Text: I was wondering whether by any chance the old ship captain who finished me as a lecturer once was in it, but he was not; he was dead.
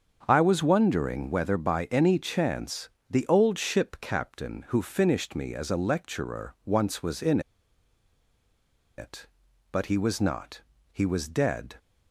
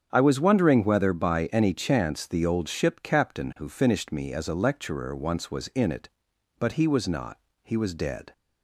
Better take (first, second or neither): second